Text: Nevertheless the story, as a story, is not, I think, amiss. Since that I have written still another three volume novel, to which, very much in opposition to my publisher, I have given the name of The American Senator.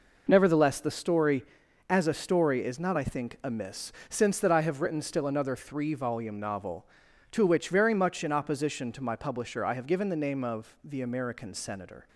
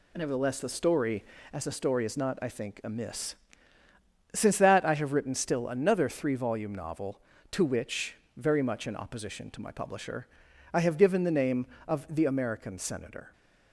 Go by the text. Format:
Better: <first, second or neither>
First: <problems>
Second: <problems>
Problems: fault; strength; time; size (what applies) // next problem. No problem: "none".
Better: neither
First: none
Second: none